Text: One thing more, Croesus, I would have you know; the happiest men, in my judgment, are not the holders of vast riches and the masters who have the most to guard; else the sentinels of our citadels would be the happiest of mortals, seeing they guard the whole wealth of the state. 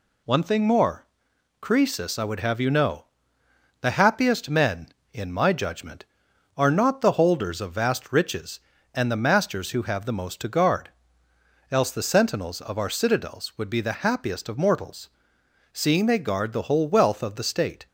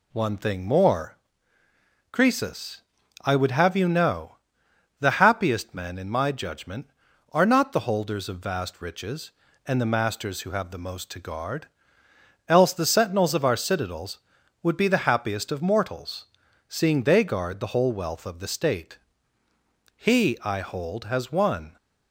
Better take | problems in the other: first | goes on to say "He I hold has won"; strong; from 19.9 s on; 1.8 s long

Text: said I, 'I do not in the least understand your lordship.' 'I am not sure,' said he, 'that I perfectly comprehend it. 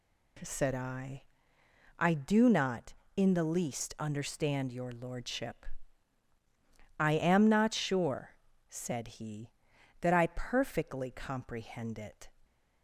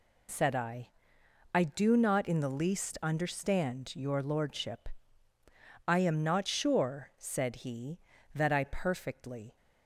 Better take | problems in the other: first | stops before "comprehend it"; at 9.5 s

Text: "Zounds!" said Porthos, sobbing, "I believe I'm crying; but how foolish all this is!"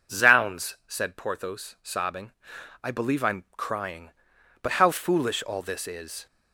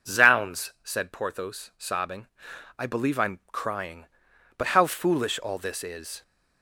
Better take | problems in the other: neither | none

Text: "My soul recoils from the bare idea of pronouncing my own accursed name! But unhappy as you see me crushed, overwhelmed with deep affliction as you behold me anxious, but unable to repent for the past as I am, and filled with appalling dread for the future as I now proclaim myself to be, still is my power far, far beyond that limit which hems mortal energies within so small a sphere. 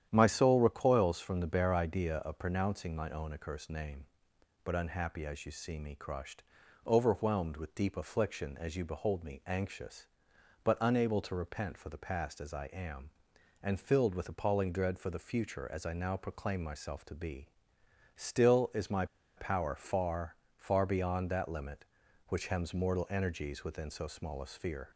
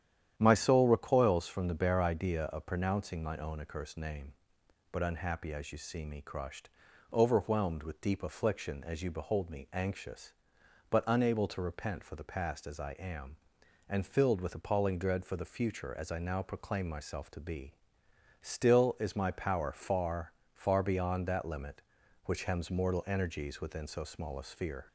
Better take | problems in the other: second | starts louder than the rest; strong; until 1.1 s; 10 dB; strong in the second // pauses between "my" and "power"; slight; at 19.0 s; 0.31 s long

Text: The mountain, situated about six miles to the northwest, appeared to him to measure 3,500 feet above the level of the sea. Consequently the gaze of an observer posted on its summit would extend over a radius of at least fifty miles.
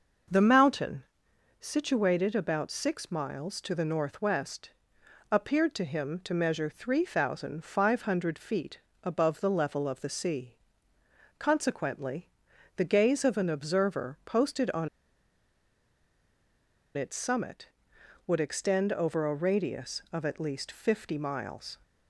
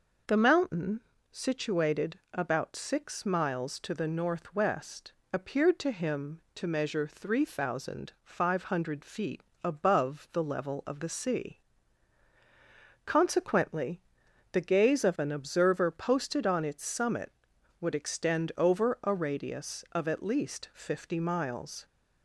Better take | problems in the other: second | pauses between "feet" and "above"; slight; at 8.7 s; 0.24 s long; slight in the second // pauses between "Consequently" and "the"; noticeable; at 12.2 s; 0.48 s long; noticeable in the second // pauses between "on" and "its"; strong; at 14.8 s; 2.0 s long

